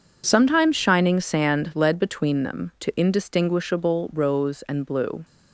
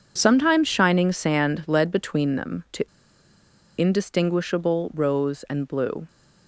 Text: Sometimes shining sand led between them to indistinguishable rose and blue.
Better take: first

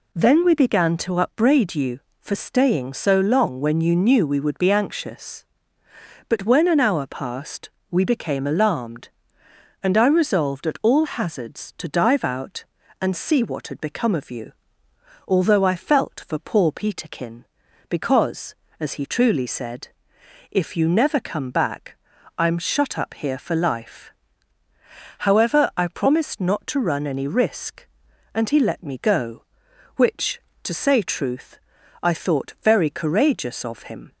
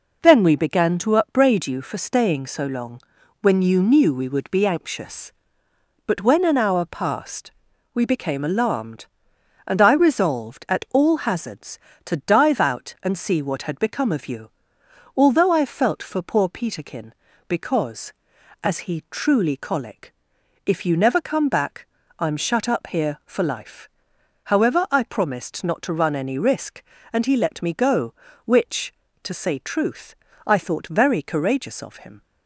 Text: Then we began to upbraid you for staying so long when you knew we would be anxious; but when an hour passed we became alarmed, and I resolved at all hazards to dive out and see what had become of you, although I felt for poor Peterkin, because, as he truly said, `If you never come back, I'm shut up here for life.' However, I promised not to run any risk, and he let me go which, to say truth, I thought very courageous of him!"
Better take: first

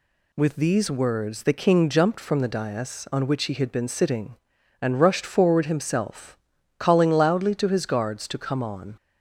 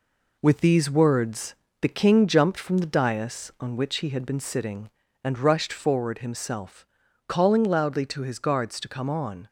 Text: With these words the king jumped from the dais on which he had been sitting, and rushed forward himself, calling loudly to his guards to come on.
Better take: first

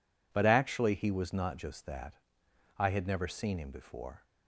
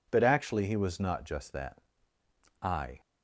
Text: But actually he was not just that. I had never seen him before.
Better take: first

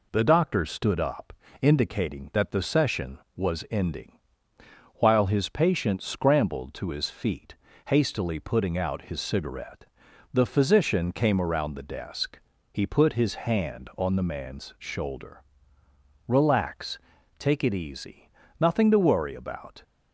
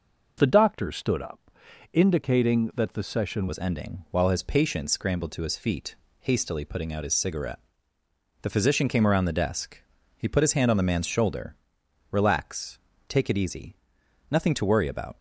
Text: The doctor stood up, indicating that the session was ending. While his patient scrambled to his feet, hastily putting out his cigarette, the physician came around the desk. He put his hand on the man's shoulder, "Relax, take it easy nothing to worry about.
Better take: first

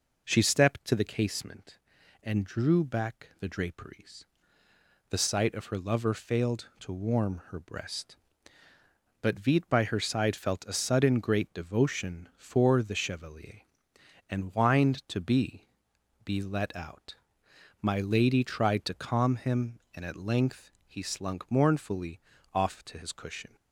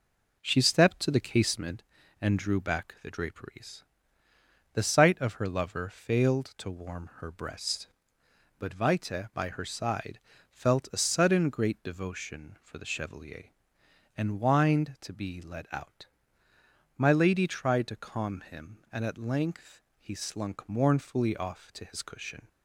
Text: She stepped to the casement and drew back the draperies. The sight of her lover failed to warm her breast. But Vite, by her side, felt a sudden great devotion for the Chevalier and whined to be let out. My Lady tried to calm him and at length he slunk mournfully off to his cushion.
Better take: second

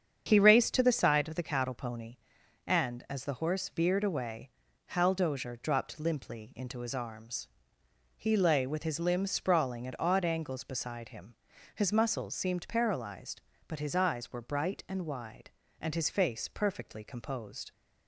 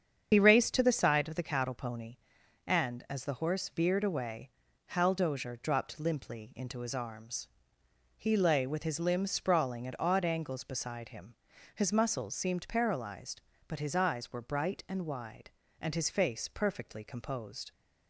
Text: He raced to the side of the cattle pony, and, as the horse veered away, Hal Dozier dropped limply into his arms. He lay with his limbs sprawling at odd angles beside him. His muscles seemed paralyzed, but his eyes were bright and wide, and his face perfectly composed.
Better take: first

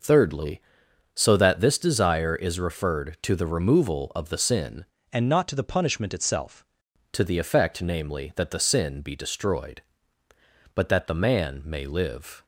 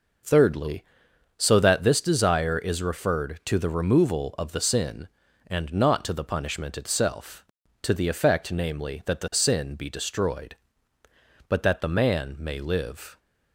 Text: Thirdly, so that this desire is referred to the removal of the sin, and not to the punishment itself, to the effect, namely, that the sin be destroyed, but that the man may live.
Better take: second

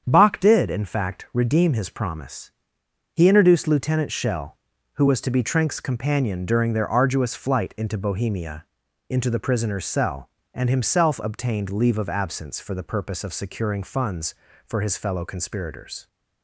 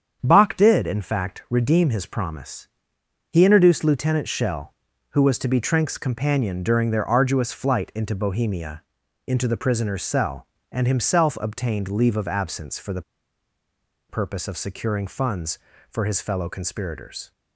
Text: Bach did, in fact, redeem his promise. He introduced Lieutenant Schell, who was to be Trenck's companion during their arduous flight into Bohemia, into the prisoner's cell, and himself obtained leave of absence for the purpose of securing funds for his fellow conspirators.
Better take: first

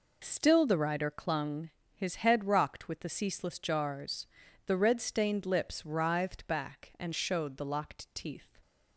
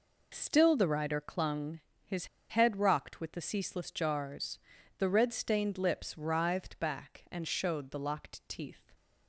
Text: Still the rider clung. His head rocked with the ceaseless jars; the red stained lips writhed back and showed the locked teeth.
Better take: first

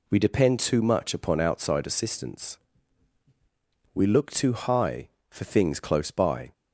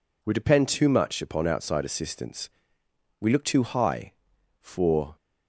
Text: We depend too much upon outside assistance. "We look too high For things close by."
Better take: first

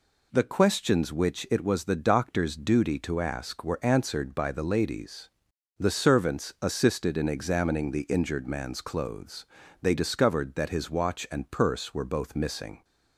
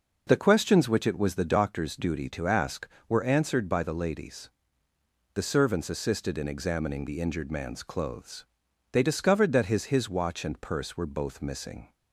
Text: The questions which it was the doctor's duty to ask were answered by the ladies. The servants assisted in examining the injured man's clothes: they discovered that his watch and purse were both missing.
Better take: first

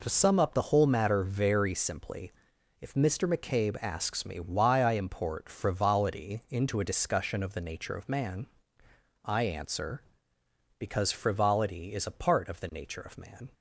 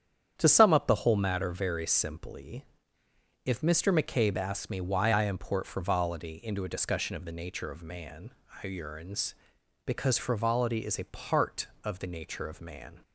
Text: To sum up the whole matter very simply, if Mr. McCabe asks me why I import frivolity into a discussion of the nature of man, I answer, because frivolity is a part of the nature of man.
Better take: first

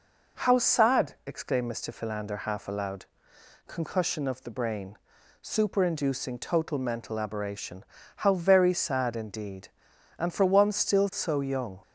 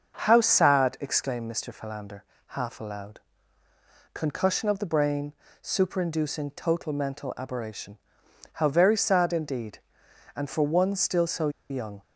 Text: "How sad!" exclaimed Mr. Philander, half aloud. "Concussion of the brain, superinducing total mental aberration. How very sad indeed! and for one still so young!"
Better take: first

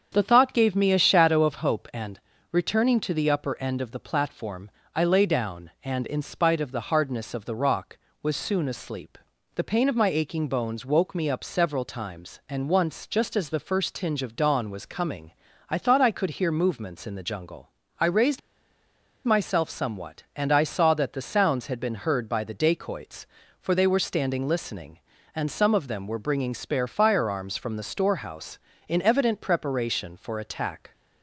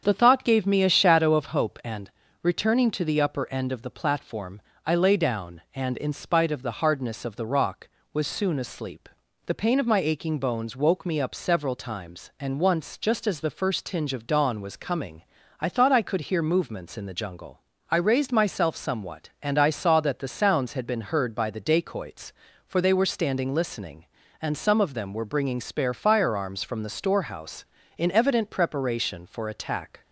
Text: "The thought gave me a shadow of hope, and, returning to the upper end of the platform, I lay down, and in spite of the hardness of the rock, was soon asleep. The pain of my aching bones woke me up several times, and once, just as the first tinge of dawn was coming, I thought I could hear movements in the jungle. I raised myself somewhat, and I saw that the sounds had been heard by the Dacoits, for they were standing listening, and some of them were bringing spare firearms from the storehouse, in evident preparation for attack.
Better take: second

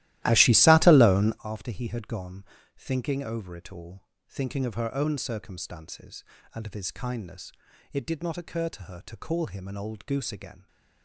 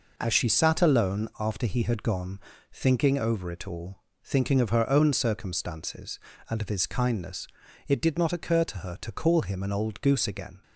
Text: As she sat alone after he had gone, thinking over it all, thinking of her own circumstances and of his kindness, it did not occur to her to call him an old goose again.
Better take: second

